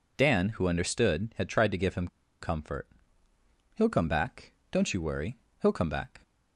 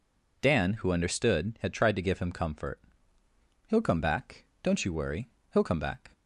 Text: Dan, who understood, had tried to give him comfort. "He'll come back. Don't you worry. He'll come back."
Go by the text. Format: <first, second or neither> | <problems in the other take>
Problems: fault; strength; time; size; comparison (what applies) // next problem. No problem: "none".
second | pauses between "him" and "comfort"; slight; at 2.0 s; 0.34 s long